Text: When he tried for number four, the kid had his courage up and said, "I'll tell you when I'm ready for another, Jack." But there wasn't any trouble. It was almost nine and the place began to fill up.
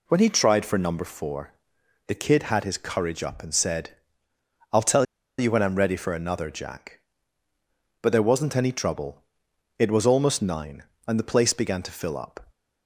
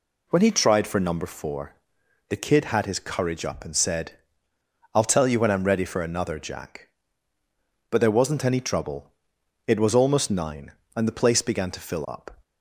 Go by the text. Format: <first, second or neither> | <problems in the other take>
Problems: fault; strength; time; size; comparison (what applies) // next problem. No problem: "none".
second | pauses between "tell" and "you"; slight; at 5.0 s; 0.34 s long